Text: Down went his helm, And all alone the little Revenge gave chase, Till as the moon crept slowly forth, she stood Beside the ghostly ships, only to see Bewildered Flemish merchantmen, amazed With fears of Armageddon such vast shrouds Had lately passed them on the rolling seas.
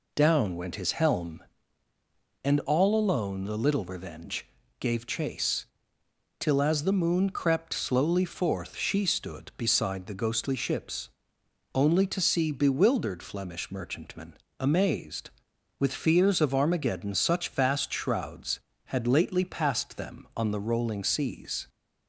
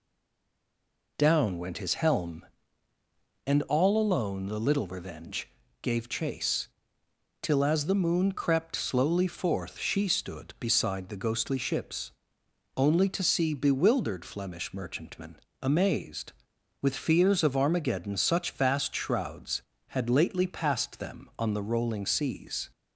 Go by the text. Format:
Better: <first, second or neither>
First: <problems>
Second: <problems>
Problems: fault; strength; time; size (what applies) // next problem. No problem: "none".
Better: first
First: pauses between "Revenge" and "gave"; slight; at 4.4 s; 0.32 s long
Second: stays silent before the first word; noticeable; until 1.1 s; 1.1 s long // pauses between "Revenge" and "gave"; slight; at 5.4 s; 0.32 s long